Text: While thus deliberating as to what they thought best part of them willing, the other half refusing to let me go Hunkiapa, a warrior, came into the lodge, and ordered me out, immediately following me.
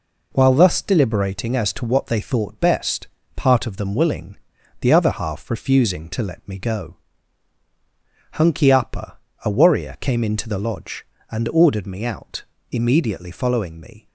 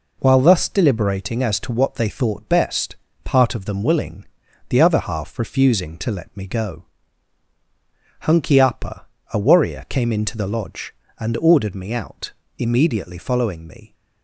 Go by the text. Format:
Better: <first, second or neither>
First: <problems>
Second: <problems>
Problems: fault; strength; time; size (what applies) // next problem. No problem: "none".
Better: neither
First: pauses between "best" and "part"; slight; at 3.0 s; 0.26 s long // pauses between "go" and "Hunkiapa"; strong; at 6.9 s; 1.4 s long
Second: pauses between "best" and "part"; slight; at 2.9 s; 0.26 s long // pauses between "go" and "Hunkiapa"; strong; at 6.8 s; 1.4 s long